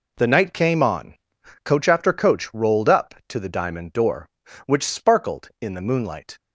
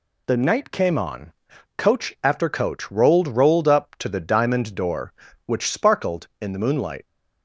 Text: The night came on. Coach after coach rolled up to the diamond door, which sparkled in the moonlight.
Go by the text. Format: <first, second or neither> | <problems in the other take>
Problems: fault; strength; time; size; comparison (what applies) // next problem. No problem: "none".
first | says "rolled" twice; at 3.2 s